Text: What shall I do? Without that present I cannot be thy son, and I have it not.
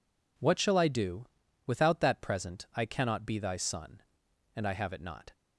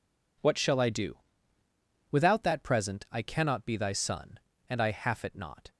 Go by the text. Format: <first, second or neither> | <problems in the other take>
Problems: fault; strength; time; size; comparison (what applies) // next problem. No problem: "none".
first | says "half" for "have"; at 4.9 s